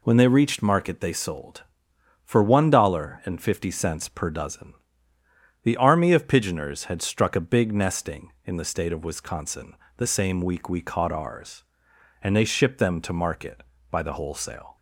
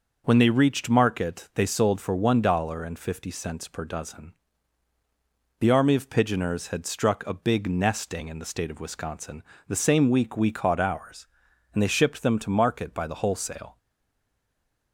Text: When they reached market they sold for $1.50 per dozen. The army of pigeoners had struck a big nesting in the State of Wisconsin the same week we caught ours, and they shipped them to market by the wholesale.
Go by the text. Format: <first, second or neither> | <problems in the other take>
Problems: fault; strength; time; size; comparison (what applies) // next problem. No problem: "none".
first | pauses between "Wisconsin" and "the"; slight; at 9.4 s; 0.24 s long; slight in the first // stays silent after the last word; noticeable; from 13.7 s on; 1.2 s long